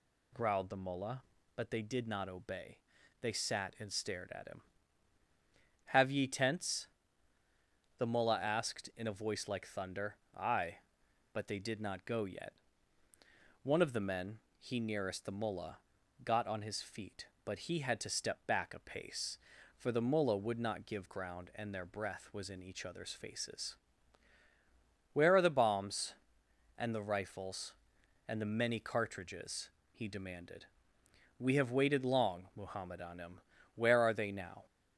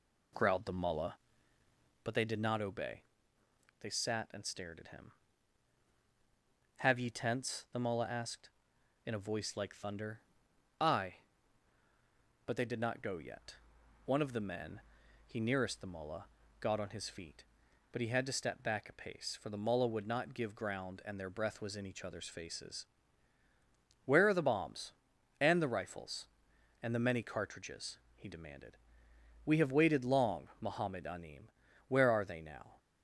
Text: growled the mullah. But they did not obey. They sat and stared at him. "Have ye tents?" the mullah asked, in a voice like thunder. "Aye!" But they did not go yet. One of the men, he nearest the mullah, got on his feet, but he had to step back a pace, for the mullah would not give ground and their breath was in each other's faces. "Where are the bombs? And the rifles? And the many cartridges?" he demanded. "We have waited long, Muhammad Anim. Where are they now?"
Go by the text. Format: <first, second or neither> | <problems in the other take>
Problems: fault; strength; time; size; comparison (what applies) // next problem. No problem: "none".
first | starts louder than the rest; slight; until 2.1 s; 2.5 dB